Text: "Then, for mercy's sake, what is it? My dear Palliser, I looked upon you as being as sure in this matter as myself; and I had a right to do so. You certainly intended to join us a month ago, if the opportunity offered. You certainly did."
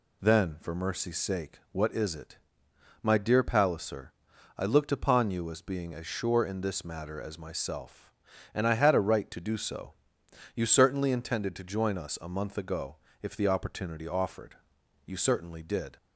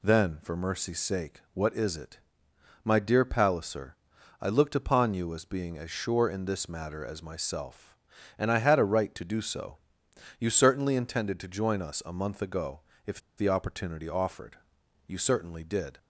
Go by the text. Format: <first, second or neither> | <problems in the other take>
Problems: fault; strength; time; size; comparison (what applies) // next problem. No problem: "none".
first | pauses between "if" and "the"; slight; at 13.1 s; 0.18 s long